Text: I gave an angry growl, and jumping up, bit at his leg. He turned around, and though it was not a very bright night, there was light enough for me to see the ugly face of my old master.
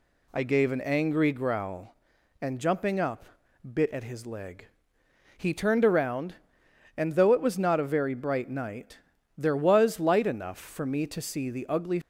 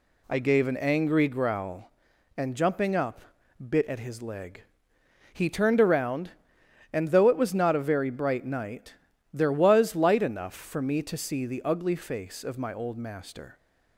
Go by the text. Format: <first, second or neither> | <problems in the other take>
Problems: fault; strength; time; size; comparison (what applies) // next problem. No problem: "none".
second | stops before "face of my old master"; at 12.0 s